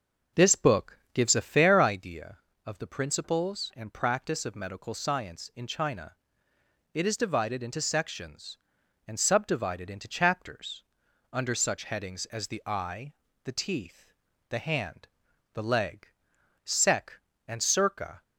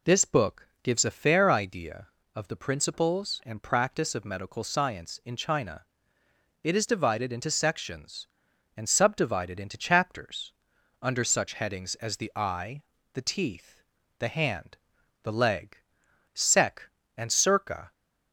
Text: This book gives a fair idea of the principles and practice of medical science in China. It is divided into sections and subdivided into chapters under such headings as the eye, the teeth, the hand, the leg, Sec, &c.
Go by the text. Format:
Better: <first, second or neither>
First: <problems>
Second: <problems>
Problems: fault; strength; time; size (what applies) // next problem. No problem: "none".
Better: second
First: starts louder than the rest; until 2.0 s; 6 dB // pauses between "chapters" and "under"; noticeable; at 10.8 s; 0.50 s long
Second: pauses between "chapters" and "under"; noticeable; at 10.5 s; 0.50 s long